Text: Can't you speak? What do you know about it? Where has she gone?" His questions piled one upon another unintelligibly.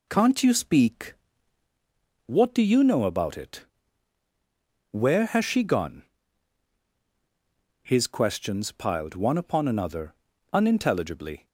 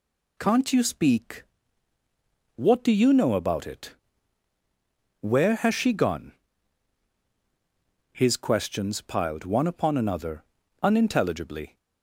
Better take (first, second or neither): second